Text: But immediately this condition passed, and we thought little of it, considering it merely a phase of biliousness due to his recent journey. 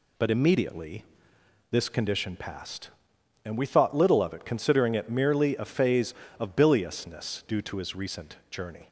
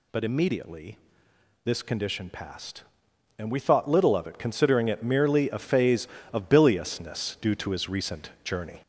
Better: first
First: pauses between "immediately" and "this"; noticeable; at 1.0 s; 0.66 s long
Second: gets louder; slight; throughout; 3.5 dB // pauses between "immediately" and "this"; noticeable; at 0.9 s; 0.66 s long

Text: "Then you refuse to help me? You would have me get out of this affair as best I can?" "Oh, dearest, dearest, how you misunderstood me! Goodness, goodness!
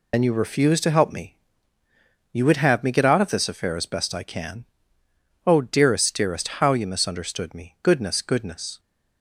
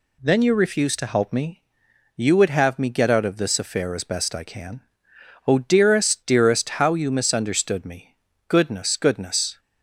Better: second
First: loses the start of "Then"; at 0.1 s; 50 ms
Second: none

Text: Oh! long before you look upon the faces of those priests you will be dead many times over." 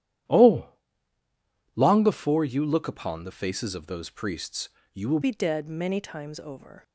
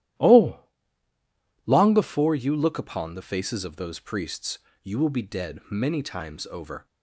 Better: second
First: starts louder than the rest; strong; until 2.3 s; 11.5 dB // pauses between "priests" and "you"; slight; at 4.6 s; 0.22 s long // changes voice at "be"; from 5.2 s on; 1.6 s long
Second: starts louder than the rest; strong; until 2.2 s; 13 dB // pauses between "priests" and "you"; slight; at 4.5 s; 0.22 s long

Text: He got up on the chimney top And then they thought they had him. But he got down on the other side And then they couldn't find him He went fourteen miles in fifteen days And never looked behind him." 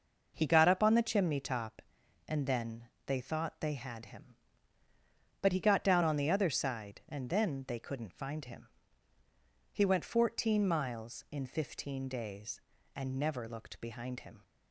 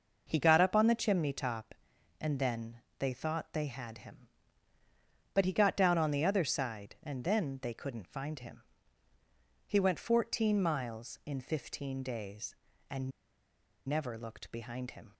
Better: first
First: pauses between "then" and "they"; slight; at 2.8 s; 0.18 s long // pauses between "him" and "He"; at 8.6 s; 1.0 s long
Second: pauses between "then" and "they"; slight; at 2.7 s; 0.18 s long // pauses between "him" and "He"; at 8.6 s; 1.0 s long // pauses between "And" and "never"; noticeable; at 13.1 s; 0.77 s long

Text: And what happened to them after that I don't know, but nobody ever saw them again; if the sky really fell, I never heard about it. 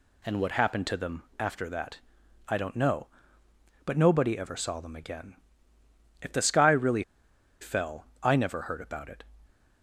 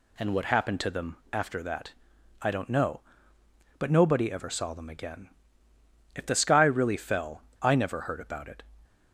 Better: second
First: pauses between "them" and "after"; slight; at 1.2 s; 0.16 s long // pauses between "that" and "I"; noticeable; at 1.9 s; 0.54 s long // pauses between "really" and "fell"; noticeable; at 7.0 s; 0.58 s long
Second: pauses between "them" and "after"; slight; at 1.1 s; 0.16 s long // pauses between "that" and "I"; noticeable; at 1.9 s; 0.54 s long

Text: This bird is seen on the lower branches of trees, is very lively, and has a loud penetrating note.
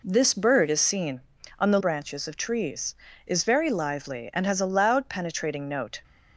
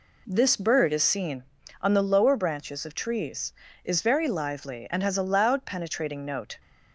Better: second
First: skips "lower"; at 1.7 s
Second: none

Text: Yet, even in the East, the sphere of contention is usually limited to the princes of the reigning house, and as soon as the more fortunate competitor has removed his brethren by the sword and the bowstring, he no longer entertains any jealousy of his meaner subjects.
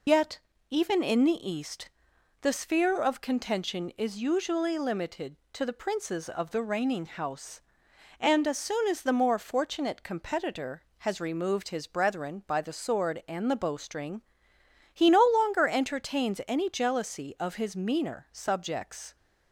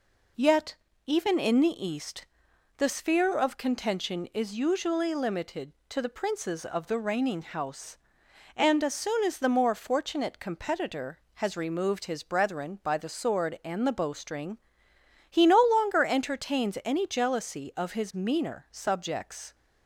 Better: second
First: loses the start of "Yet"; at 0.0 s; 65 ms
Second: none

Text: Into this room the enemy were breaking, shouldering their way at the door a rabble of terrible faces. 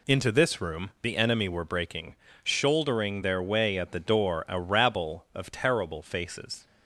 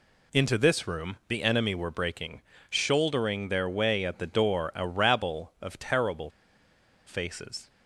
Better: first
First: none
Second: pauses between "terrible" and "faces"; noticeable; at 6.2 s; 0.76 s long

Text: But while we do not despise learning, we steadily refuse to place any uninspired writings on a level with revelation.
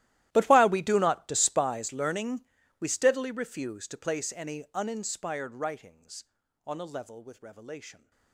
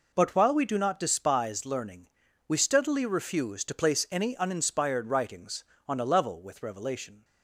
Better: second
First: gets quieter; strong; throughout; 21.5 dB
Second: none

